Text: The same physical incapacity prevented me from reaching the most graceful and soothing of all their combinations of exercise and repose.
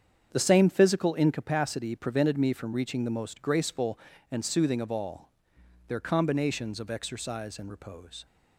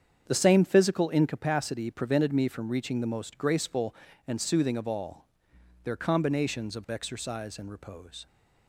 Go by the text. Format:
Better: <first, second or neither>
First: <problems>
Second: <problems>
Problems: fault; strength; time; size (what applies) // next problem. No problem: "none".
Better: neither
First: starts louder than the rest; strong; until 1.3 s; 8 dB // pauses between "all" and "their"; noticeable; at 5.2 s; 0.60 s long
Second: starts louder than the rest; strong; until 1.2 s; 8 dB // pauses between "all" and "their"; noticeable; at 5.2 s; 0.60 s long